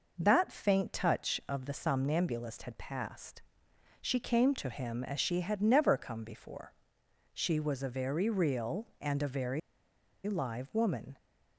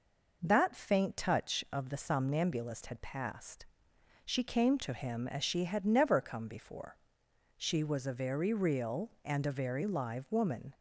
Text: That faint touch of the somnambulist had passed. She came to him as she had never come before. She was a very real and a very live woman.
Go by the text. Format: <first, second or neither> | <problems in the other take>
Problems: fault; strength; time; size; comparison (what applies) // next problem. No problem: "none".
second | pauses between "very" and "live"; noticeable; at 9.5 s; 0.66 s long